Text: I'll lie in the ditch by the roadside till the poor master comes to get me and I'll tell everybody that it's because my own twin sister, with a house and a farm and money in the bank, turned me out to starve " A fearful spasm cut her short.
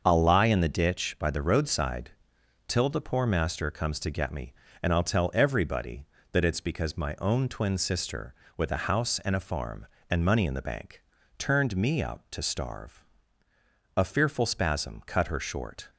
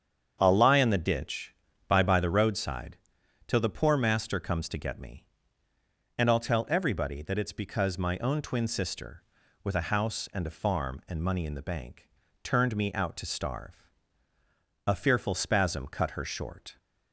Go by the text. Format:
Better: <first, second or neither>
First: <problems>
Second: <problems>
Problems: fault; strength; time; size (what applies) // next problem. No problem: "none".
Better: first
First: starts louder than the rest; until 1.0 s; 6.5 dB // pauses between "roadside" and "till"; noticeable; at 2.0 s; 0.56 s long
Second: starts louder than the rest; strong; until 1.4 s; 7.5 dB // says "by" twice; at 2.0 s // pauses between "roadside" and "till"; noticeable; at 2.9 s; 0.50 s long